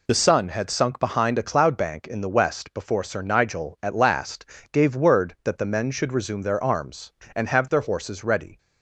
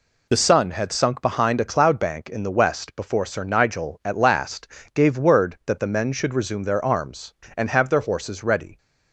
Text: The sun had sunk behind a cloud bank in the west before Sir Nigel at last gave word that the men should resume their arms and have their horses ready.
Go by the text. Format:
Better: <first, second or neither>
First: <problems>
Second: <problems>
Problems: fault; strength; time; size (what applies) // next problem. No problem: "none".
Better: neither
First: pauses between "last" and "gave"; slight; at 4.4 s; 0.26 s long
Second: pauses between "last" and "gave"; slight; at 4.6 s; 0.26 s long